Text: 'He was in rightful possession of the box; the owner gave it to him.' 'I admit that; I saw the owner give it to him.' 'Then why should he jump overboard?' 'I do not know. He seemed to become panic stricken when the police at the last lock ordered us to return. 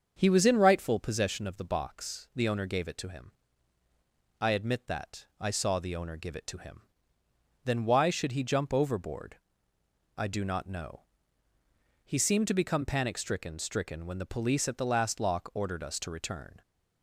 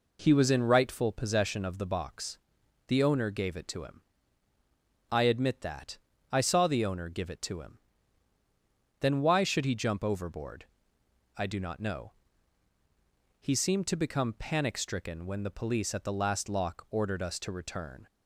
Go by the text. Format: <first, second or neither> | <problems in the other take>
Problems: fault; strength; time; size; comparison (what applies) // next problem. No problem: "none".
second | starts louder than the rest; until 1.2 s; 7 dB // says "stricken" twice; at 13.5 s